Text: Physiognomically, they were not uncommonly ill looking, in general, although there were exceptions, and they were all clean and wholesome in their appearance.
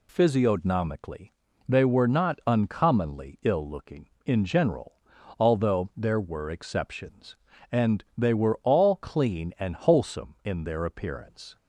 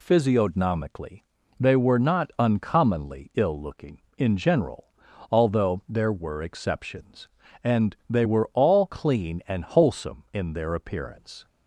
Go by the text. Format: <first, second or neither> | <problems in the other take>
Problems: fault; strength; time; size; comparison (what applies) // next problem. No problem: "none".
neither | none